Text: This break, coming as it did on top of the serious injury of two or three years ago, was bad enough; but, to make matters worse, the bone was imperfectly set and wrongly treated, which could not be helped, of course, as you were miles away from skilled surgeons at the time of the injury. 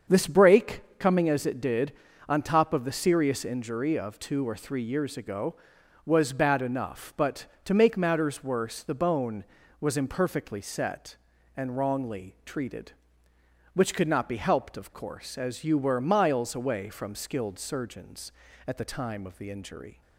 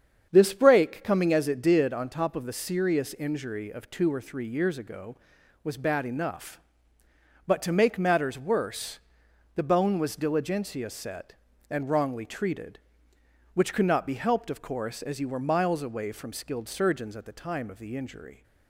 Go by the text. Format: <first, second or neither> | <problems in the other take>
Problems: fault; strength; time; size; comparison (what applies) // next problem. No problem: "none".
first | starts louder than the rest; strong; until 1.3 s; 7.5 dB; also in the first // says "diligentia" for "imperfectly"; at 10.1 s